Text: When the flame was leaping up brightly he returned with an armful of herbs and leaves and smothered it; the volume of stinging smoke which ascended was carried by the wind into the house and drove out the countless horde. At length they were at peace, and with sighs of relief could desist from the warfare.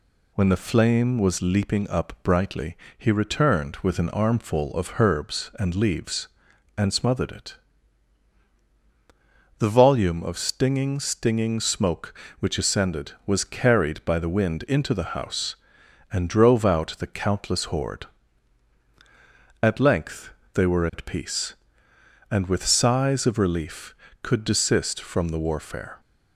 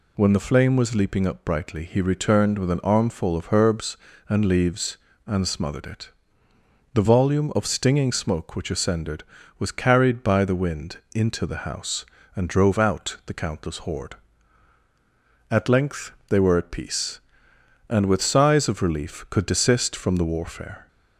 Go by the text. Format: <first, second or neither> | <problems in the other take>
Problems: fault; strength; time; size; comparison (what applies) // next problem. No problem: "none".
second | pauses between "brightly" and "he"; slight; at 2.7 s; 0.22 s long // says "stinging" twice; at 10.9 s // pauses between "length" and "they"; slight; at 20.3 s; 0.24 s long; slight in the second